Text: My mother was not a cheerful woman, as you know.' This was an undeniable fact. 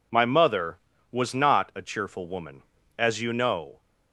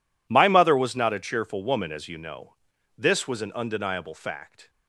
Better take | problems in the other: second | stops before "This was an undeniable fact"; at 3.8 s

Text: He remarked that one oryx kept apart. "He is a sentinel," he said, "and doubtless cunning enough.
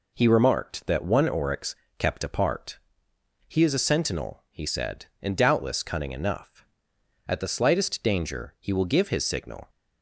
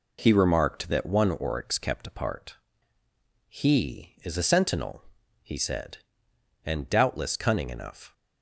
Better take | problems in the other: second | pauses between "oryx" and "kept"; slight; at 1.7 s; 0.24 s long // goes on to say "At the slightest danger he will give his signal"; strong; from 7.2 s on; 2.4 s long

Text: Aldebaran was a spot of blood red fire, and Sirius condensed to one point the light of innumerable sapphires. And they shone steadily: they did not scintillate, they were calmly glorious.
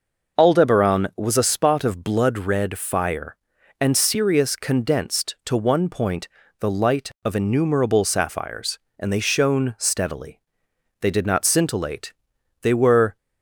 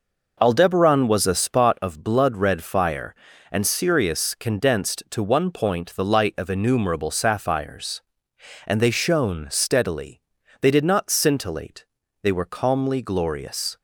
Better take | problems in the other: second | pauses between "point" and "the"; slight; at 6.2 s; 0.32 s long // stops before "calmly glorious"; at 13.1 s

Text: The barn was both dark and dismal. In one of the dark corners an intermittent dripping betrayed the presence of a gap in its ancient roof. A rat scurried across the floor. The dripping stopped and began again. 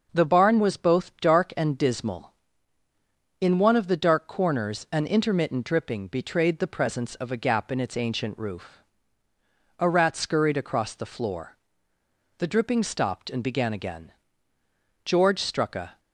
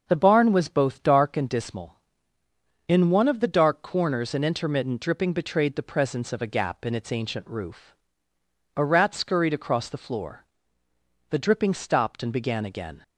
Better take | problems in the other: second | starts louder than the rest; until 1.1 s; 6.5 dB; noticeable in the second // goes on to say "George struck a"; noticeable; from 15.0 s on; 0.94 s long

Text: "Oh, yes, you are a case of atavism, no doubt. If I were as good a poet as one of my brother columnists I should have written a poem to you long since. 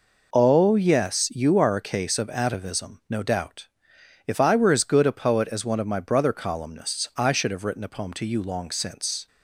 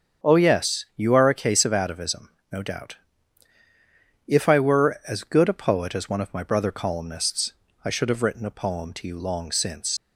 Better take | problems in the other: first | starts louder than the rest; strong; until 1.3 s; 7.5 dB // pauses between "columnists" and "I"; slight; at 7.5 s; 0.30 s long // leaves "since" unfinished; at 9.9 s; 120 ms

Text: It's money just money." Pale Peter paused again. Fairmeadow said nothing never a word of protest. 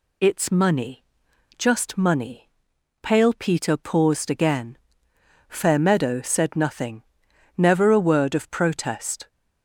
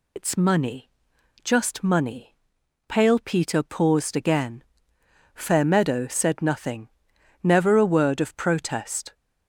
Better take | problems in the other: first | loses the start of "It's"; at 0.1 s; 85 ms // pauses between "money" and "just"; noticeable; at 0.8 s; 0.54 s long; noticeable in the first // pauses between "nothing" and "never"; noticeable; at 6.8 s; 0.54 s long; noticeable in the first

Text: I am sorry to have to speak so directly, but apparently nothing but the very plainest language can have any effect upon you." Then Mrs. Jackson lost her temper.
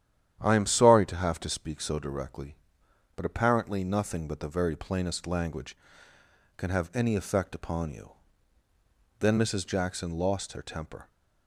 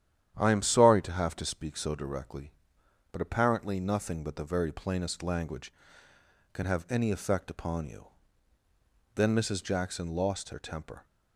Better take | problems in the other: neither | starts louder than the rest; strong; the same in both

